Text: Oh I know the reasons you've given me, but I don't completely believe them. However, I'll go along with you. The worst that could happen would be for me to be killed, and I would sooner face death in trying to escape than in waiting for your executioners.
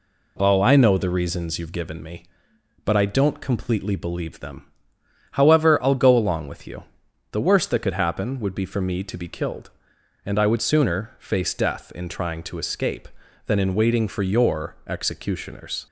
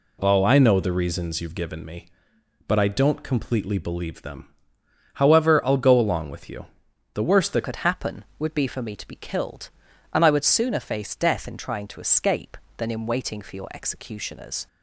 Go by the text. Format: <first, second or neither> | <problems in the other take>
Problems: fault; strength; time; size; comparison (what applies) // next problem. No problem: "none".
first | changes voice at "could"; from 7.6 s on; 7.0 s long